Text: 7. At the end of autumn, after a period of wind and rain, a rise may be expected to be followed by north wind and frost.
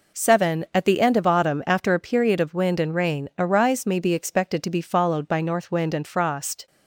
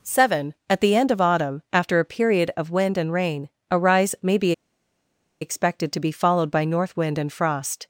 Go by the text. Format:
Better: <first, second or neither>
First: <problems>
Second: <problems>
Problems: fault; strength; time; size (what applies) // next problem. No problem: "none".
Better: first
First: none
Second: pauses between "be" and "expected"; noticeable; at 4.5 s; 0.89 s long